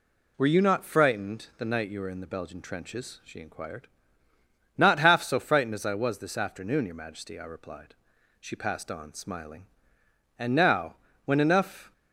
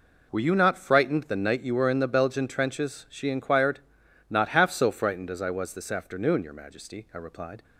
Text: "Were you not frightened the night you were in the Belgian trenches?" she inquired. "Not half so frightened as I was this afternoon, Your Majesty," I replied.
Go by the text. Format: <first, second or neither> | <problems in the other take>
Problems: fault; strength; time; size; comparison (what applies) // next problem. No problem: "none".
second | goes on to say "She passed on smiling And now when enough"; strong; from 8.4 s on; 3.5 s long